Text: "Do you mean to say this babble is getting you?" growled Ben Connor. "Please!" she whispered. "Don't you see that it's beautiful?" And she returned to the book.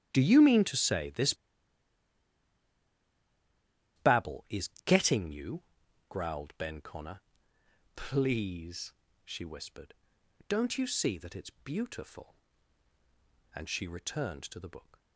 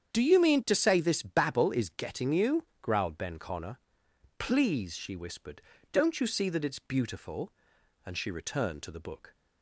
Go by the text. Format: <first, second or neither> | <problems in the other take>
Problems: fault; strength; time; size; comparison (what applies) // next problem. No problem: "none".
second | starts louder than the rest; strong; until 1.1 s; 10 dB; strong in the second // pauses between "this" and "babble"; strong; at 1.3 s; 2.6 s long // pauses between "is" and "getting"; slight; at 4.6 s; 0.16 s long